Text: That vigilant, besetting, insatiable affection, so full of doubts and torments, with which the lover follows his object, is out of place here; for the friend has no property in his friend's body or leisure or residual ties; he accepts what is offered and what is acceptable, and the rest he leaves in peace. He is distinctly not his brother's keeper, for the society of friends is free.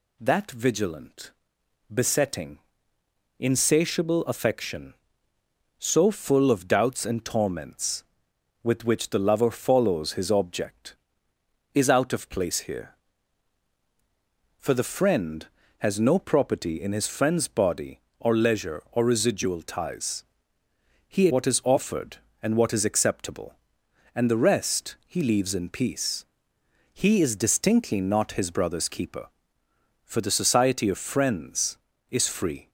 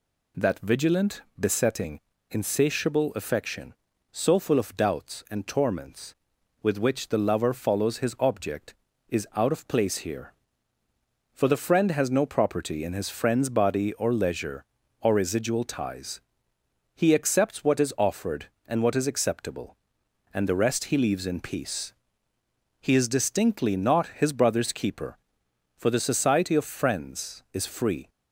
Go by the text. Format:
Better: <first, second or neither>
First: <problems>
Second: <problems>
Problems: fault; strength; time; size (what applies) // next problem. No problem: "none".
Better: second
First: skips "accepts"; at 21.2 s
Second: none